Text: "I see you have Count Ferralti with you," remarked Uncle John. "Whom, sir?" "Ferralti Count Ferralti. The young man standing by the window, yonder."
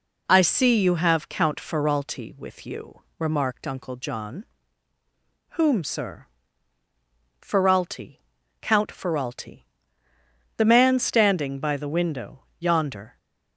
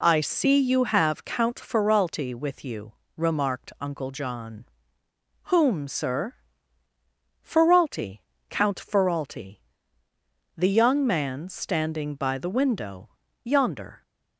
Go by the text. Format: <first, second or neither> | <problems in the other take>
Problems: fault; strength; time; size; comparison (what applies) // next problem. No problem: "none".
second | pauses between "Ferralti" and "Count"; at 8.1 s; 0.42 s long; slight in the second // skips "young"; at 10.6 s